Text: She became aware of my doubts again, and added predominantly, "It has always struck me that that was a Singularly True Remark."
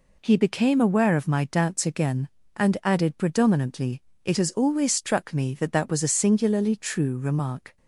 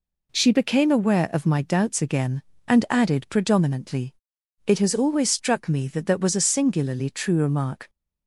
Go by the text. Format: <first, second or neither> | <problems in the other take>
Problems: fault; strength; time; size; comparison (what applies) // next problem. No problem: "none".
second | says "He" for "She"; at 0.2 s